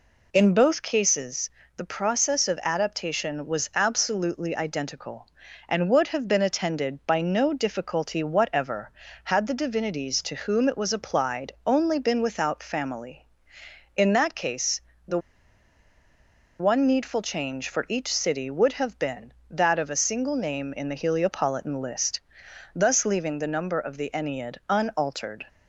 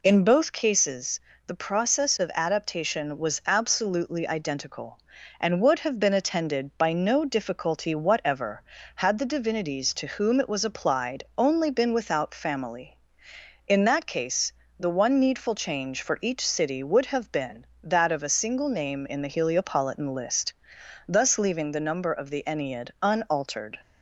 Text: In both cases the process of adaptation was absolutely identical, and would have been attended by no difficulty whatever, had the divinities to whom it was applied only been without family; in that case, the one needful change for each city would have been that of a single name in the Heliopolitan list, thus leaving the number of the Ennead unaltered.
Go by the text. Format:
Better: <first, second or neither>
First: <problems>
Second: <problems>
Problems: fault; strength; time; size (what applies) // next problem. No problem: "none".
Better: second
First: pauses between "cases" and "the"; slight; at 1.5 s; 0.24 s long // pauses between "applied" and "only"; slight; at 11.5 s; 0.16 s long // pauses between "the" and "one"; strong; at 15.1 s; 1.4 s long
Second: pauses between "cases" and "the"; slight; at 1.2 s; 0.24 s long // pauses between "applied" and "only"; slight; at 11.2 s; 0.16 s long